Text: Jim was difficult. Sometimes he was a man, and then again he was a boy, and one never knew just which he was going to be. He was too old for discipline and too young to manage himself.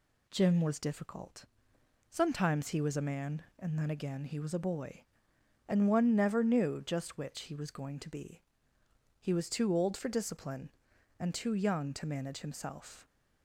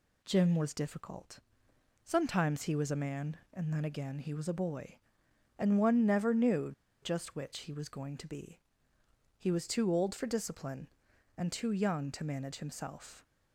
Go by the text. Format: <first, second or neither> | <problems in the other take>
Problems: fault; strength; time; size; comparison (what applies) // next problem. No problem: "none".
first | pauses between "knew" and "just"; slight; at 6.7 s; 0.30 s long